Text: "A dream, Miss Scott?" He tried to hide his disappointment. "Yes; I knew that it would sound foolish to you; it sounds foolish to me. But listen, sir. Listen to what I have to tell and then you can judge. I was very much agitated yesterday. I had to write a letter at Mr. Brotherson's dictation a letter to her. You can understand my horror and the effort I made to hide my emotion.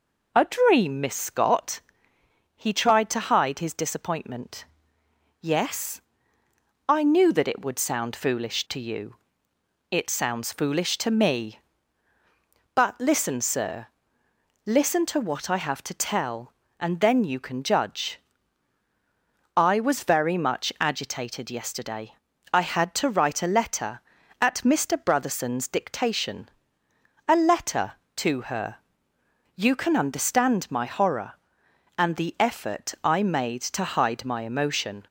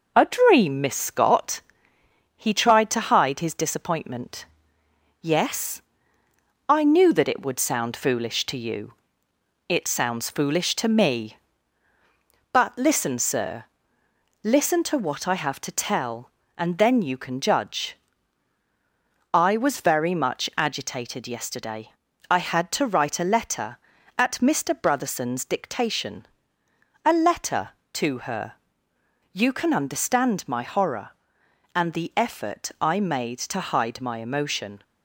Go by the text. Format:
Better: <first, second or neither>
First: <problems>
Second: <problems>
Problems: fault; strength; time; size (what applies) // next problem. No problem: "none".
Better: first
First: pauses between "dictation" and "a"; noticeable; at 26.4 s; 0.80 s long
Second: gets quieter; slight; throughout; 3 dB // pauses between "dictation" and "a"; noticeable; at 26.2 s; 0.80 s long